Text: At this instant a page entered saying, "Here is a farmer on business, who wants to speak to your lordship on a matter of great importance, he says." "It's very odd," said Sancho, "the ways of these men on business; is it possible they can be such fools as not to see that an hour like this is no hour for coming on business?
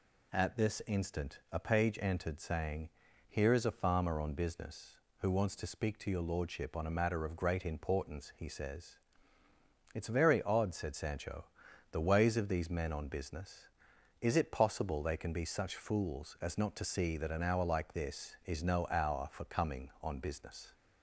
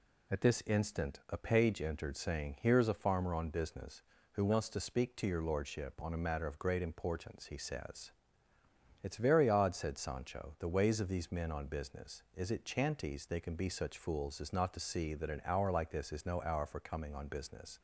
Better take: first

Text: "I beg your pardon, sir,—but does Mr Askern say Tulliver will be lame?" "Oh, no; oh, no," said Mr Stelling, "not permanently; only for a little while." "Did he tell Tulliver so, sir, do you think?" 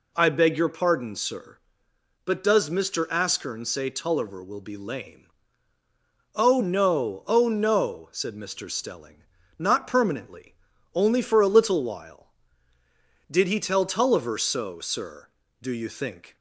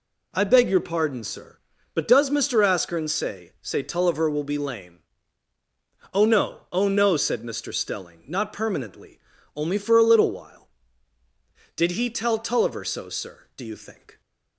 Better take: first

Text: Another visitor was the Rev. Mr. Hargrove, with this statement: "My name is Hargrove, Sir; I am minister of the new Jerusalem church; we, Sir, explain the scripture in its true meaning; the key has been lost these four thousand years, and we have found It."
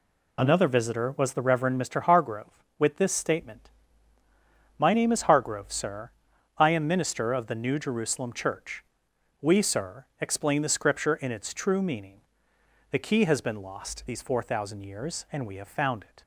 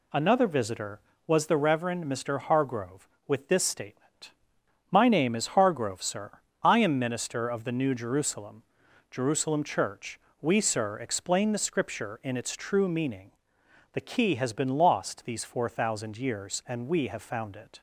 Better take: first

